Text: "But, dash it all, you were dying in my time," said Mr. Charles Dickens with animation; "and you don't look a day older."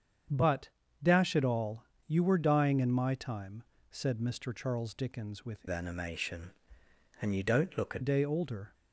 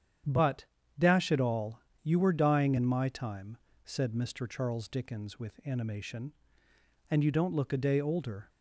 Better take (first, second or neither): second